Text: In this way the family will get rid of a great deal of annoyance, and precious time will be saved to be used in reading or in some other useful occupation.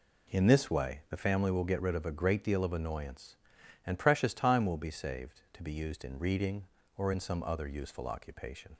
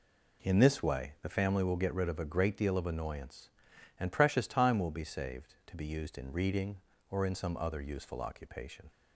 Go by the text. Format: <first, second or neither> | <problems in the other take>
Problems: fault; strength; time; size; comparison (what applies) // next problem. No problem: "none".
neither | none